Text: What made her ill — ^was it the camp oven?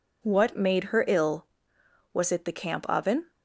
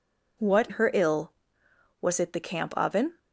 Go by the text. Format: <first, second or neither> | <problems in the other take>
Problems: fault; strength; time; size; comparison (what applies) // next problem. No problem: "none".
first | skips "made"; at 0.7 s